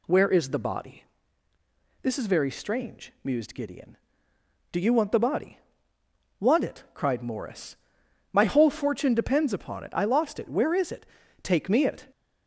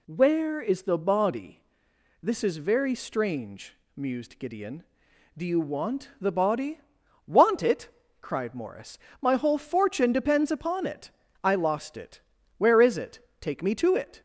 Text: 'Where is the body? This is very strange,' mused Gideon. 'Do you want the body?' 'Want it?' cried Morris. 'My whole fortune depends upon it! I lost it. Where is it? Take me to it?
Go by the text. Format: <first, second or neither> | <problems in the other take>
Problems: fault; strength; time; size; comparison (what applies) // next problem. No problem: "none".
second | skips "to"; at 11.8 s